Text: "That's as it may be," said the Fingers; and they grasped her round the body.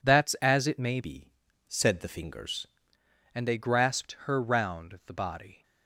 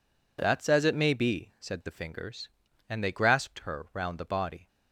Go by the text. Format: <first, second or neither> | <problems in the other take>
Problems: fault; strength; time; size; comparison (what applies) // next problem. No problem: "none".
second | changes voice from "be" to "Fingers"; from 0.9 to 2.6 s; 1.7 s long